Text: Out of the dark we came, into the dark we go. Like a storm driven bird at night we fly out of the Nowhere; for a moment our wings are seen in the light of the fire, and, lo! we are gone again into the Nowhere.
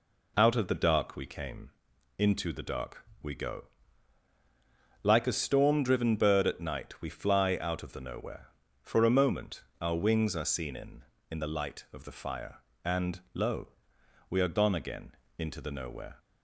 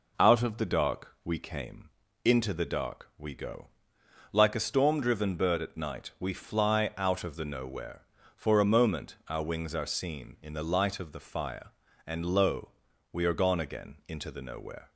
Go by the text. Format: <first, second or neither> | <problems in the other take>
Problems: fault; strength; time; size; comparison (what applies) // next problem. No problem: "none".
second | pauses between "dark" and "we"; slight; at 3.0 s; 0.18 s long // pauses between "moment" and "our"; slight; at 9.6 s; 0.18 s long // says "in" twice; at 11.3 s // pauses between "again" and "into"; slight; at 15.1 s; 0.26 s long